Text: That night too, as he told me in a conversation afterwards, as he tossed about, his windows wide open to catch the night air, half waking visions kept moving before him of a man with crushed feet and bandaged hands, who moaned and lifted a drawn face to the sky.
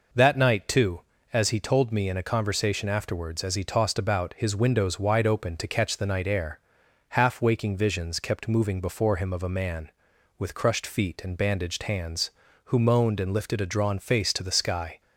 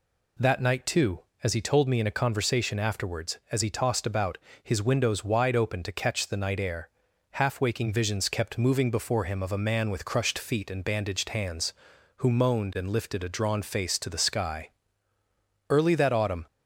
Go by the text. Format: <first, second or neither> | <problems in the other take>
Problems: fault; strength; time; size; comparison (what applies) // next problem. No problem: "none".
first | goes on to say "Early that autumn"; noticeable; from 15.6 s on; 0.76 s long